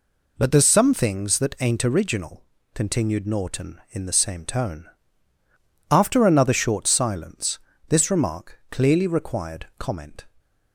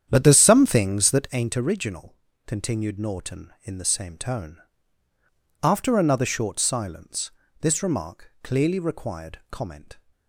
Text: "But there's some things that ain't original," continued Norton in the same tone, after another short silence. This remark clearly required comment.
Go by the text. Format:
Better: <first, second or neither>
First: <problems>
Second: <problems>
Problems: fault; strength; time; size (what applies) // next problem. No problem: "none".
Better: first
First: none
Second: starts louder than the rest; strong; until 1.4 s; 9.5 dB